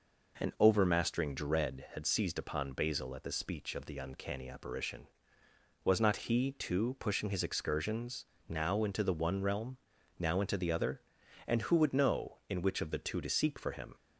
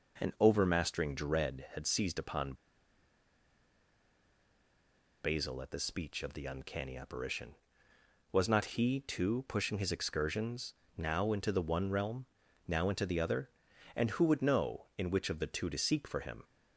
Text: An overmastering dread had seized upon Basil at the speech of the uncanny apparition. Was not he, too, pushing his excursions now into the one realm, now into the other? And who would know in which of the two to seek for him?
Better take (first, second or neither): first